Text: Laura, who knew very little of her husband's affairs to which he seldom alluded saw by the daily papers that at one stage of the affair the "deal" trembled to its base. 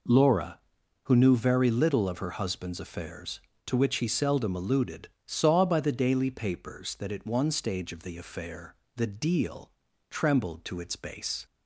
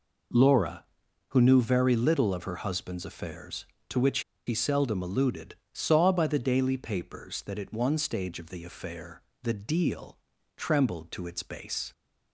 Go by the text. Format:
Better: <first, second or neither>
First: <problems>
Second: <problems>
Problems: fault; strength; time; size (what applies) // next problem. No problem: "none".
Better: first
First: pauses between "alluded" and "saw"; slight; at 5.0 s; 0.20 s long // pauses between "affair" and "the"; slight; at 8.7 s; 0.22 s long // pauses between "deal" and "trembled"; at 9.6 s; 0.40 s long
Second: pauses between "which" and "he"; slight; at 4.1 s; 0.26 s long // pauses between "alluded" and "saw"; slight; at 5.5 s; 0.20 s long // pauses between "affair" and "the"; slight; at 9.1 s; 0.22 s long // pauses between "deal" and "trembled"; at 10.1 s; 0.40 s long